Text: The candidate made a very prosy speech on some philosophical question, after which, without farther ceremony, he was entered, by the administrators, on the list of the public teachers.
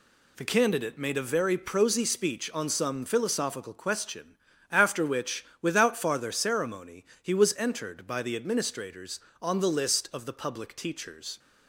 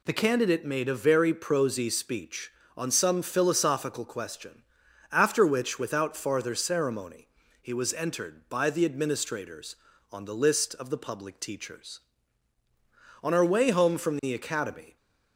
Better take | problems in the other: first | goes on to say "On our way home from the academy"; strong; from 13.2 s on; 1.7 s long

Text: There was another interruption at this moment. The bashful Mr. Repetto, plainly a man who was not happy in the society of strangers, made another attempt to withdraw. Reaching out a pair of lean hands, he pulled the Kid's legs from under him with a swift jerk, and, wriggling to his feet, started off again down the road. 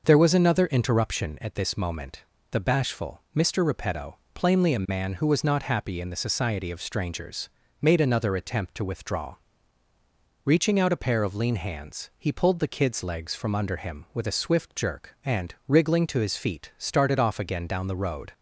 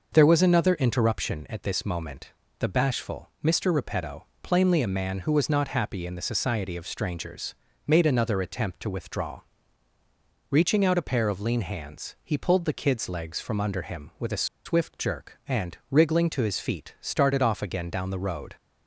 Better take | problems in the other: first | pauses between "a" and "swift"; slight; at 14.4 s; 0.20 s long

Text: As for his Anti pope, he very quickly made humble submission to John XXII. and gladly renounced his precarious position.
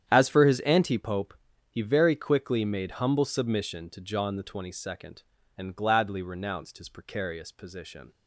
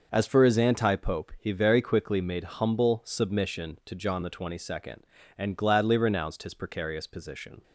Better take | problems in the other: second | starts louder than the rest; strong; until 1.0 s; 9.5 dB

